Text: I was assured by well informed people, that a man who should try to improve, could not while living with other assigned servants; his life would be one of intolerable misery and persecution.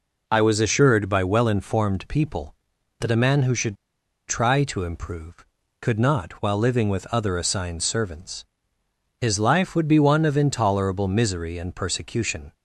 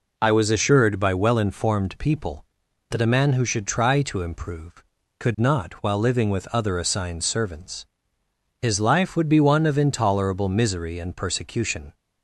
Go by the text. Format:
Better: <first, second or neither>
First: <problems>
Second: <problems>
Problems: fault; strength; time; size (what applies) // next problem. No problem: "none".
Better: second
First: pauses between "should" and "try"; noticeable; at 3.7 s; 0.52 s long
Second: none